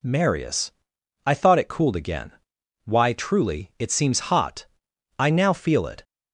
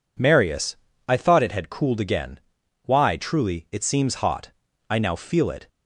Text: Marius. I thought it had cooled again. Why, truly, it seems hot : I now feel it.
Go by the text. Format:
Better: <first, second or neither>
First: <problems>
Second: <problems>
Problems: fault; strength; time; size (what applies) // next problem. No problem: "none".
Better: second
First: skips "had"; at 1.6 s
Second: none